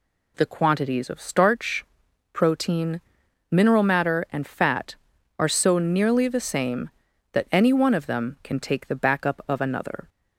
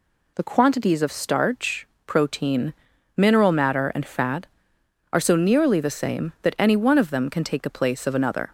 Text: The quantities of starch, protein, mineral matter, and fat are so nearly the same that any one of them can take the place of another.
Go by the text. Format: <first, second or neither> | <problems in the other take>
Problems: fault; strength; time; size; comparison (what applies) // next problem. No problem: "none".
second | says "backup" for "place"; at 8.9 s